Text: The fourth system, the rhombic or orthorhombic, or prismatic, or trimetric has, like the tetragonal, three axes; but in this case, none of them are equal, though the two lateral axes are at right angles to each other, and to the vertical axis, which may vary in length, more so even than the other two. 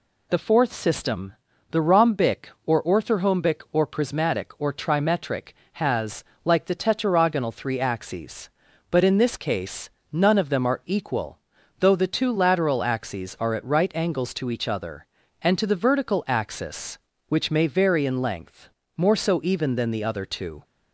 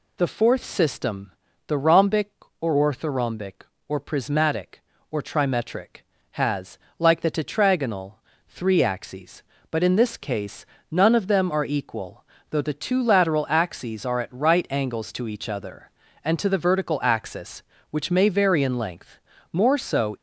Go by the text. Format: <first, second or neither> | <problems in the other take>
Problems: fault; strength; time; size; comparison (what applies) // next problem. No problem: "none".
first | stops before "even than the other two"; at 20.1 s